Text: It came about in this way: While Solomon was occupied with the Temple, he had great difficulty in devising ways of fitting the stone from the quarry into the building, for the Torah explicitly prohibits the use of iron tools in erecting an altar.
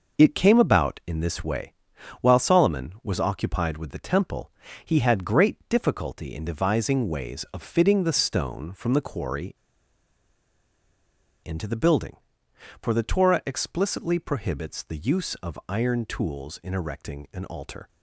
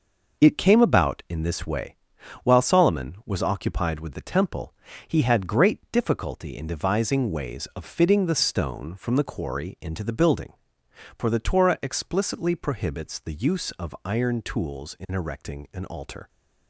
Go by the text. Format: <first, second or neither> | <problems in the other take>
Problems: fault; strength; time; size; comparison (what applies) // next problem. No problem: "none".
second | pauses between "quarry" and "into"; strong; at 9.5 s; 1.8 s long